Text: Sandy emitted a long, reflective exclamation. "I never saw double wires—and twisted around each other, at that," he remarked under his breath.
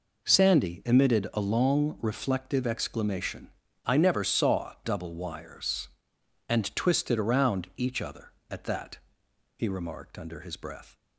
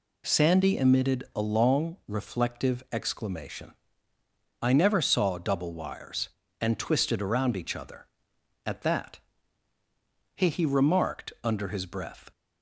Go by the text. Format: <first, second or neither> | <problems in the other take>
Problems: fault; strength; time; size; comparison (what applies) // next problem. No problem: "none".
first | says "he" twice; at 10.4 s